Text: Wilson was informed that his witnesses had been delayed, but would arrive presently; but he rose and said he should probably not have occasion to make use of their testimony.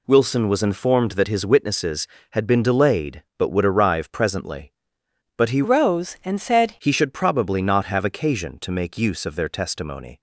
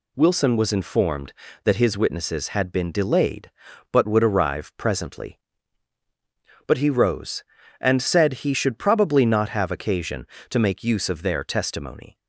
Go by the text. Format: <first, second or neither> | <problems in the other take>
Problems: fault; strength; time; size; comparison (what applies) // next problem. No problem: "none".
second | changes voice from "rose" to "said"; from 5.6 to 6.7 s; 1.1 s long